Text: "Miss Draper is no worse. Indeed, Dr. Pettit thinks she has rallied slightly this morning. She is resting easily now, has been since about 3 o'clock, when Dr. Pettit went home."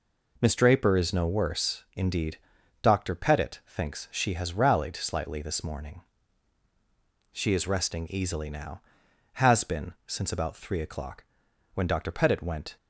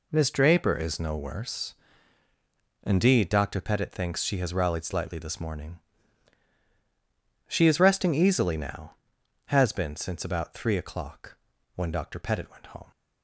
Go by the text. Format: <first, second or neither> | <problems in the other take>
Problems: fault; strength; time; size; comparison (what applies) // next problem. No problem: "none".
second | stops before "home"; at 12.7 s